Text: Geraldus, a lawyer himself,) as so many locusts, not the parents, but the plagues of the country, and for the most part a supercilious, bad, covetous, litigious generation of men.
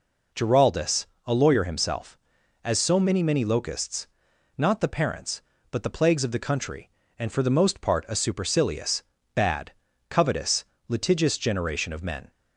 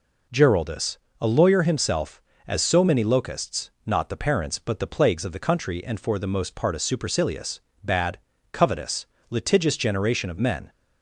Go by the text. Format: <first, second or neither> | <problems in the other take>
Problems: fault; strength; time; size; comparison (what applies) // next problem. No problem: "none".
second | says "many" twice; at 3.2 s